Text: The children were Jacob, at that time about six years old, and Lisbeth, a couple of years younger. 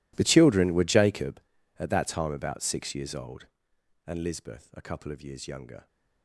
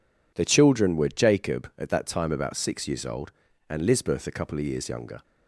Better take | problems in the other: second | gets quieter; strong; throughout; 21.5 dB

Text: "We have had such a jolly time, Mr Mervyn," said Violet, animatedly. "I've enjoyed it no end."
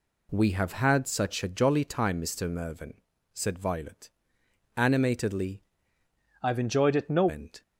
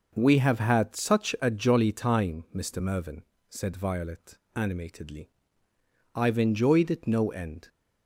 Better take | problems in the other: second | changes voice from "I've" to "no"; from 6.4 to 7.2 s; 0.8 s long

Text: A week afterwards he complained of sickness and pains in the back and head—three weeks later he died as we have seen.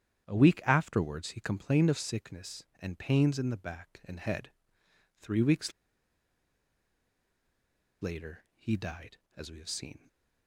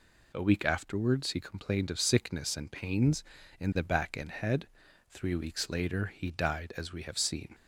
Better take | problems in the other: second | starts louder than the rest; strong; until 1.3 s; 9.5 dB // pauses between "weeks" and "later"; strong; at 5.7 s; 2.2 s long

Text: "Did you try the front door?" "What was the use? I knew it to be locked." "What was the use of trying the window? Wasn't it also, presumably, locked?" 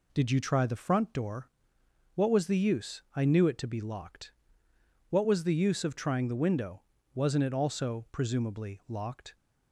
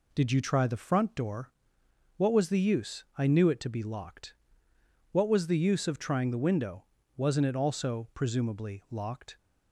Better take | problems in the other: neither | none

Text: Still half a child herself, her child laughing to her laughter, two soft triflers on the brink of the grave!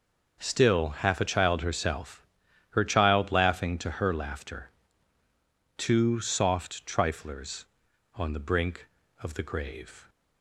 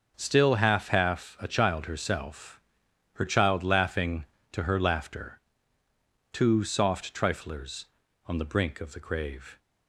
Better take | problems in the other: first | starts louder than the rest; until 1.1 s; 6 dB; also in the first // says "half" twice; at 0.8 s

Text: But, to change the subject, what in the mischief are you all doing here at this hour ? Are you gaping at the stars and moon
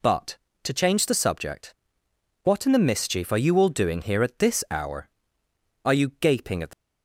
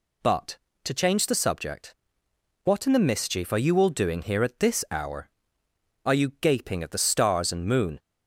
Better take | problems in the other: second | stops before "stars and moon"; at 6.7 s

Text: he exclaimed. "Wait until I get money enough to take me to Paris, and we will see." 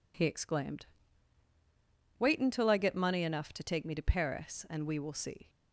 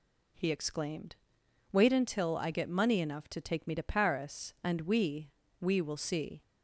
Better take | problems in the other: first | says "we" twice; at 5.6 s

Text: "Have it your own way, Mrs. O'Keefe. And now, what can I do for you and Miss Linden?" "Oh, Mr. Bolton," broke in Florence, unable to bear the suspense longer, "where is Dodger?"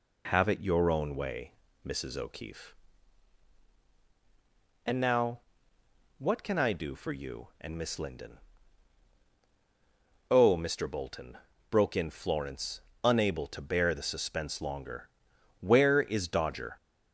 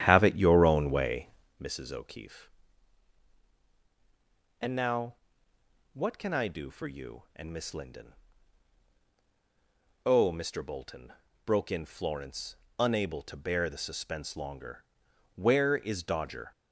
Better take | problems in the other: first | starts louder than the rest; strong; until 1.6 s; 10.5 dB

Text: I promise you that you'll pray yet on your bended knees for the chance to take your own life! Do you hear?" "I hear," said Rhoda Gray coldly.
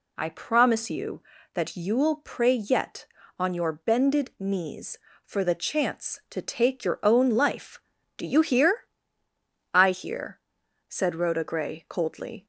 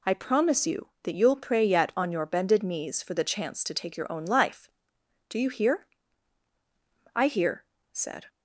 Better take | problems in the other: first | stops before "Rhoda Gray coldly"; at 8.2 s

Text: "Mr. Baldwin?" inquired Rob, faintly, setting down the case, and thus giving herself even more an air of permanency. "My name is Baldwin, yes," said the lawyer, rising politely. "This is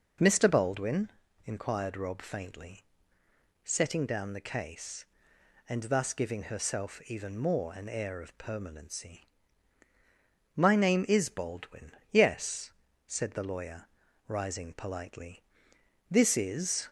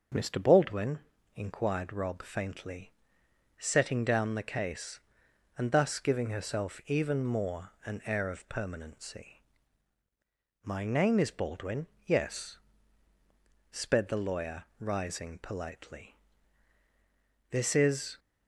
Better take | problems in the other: first | starts louder than the rest; until 1.4 s; 6 dB // says "sped" for "said"; at 13.7 s

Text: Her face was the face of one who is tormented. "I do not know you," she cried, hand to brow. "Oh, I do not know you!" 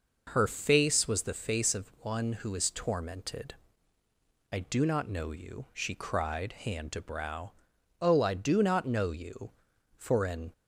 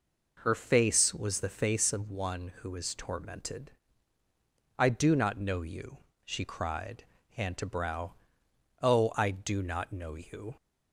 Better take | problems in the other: second | goes on to say "For an"; from 9.9 s on; 0.56 s long

